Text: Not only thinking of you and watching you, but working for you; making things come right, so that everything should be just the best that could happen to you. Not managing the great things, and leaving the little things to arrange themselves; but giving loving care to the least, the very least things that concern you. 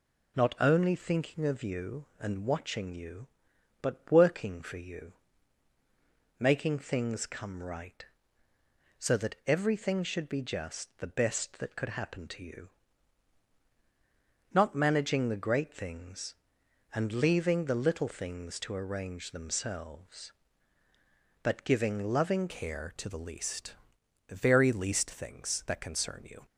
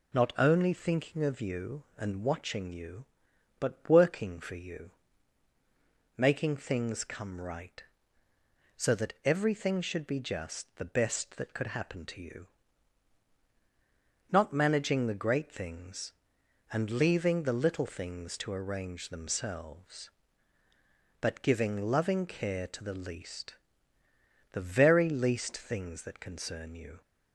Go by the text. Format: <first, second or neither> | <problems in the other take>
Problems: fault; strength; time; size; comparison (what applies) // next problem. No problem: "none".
second | changes voice at "care"; from 22.4 s on; 4.0 s long